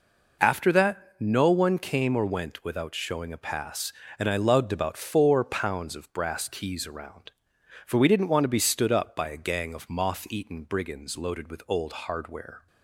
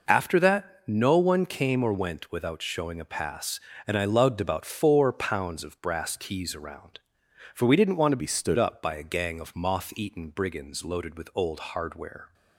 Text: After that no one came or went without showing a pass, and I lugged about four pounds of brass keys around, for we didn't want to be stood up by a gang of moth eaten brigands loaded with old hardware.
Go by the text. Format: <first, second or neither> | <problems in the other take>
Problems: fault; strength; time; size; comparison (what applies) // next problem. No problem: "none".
first | pauses between "that" and "no"; slight; at 0.7 s; 0.16 s long; slight in the first // changes voice from "be" to "stood"; from 8.2 to 8.5 s; 0.3 s long